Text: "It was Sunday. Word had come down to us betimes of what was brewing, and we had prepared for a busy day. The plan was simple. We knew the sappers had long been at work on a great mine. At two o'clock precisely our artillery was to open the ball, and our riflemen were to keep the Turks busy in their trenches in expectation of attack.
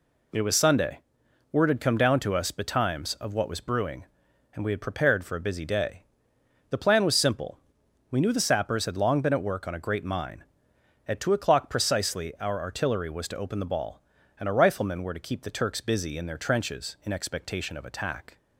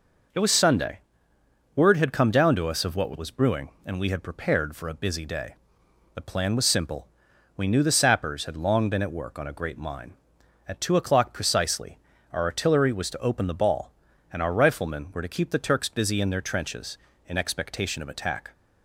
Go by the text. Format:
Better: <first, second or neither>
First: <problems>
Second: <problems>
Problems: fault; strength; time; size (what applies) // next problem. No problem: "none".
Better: first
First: none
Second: skips "betimes"; at 2.8 s // pauses between "precisely" and "our"; slight; at 11.9 s; 0.34 s long